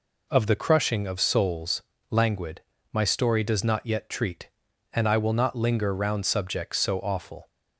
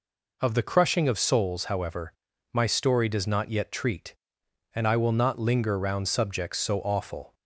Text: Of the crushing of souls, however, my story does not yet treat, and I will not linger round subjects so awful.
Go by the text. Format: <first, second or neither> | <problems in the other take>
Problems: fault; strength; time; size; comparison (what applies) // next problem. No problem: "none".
second | says "languid" for "however"; at 2.0 s